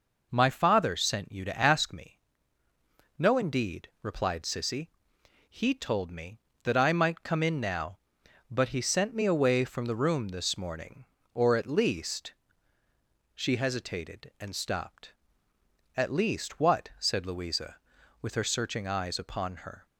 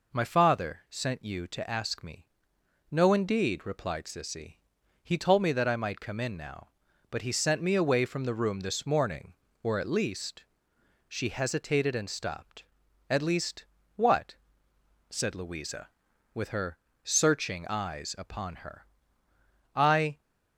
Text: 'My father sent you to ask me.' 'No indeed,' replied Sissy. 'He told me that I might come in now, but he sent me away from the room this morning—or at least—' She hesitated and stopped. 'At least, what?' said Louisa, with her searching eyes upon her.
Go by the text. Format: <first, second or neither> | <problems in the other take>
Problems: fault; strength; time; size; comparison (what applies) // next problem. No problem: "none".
first | pauses between "her" and "searching"; slight; at 16.7 s; 0.26 s long // goes on to say "I"; slight; from 19.7 s on; 0.44 s long